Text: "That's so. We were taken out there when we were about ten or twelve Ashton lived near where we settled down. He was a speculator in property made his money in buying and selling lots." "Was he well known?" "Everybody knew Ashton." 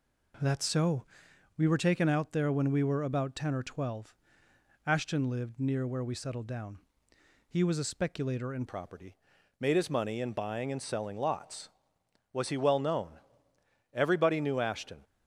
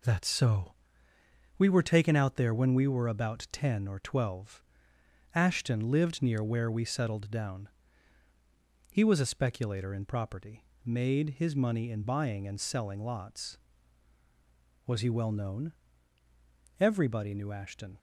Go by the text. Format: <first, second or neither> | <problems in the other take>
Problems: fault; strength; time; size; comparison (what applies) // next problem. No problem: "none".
second | pauses between "twelve" and "Ashton"; noticeable; at 4.1 s; 0.72 s long; noticeable in the second // changes voice at "property"; from 8.6 s on; 6.4 s long // pauses between "property" and "made"; noticeable; at 9.1 s; 0.46 s long; slight in the second